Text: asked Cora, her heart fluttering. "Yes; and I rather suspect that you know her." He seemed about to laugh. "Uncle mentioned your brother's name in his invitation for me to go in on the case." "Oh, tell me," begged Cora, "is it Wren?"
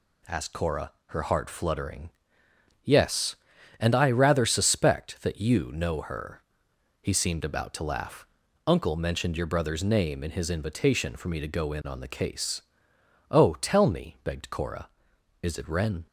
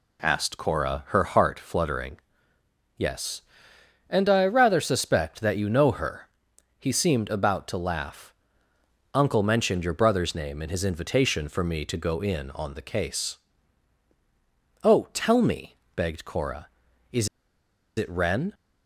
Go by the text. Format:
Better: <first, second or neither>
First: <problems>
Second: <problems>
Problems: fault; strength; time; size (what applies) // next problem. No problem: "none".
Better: first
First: none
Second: pauses between "is" and "it"; noticeable; at 17.2 s; 0.69 s long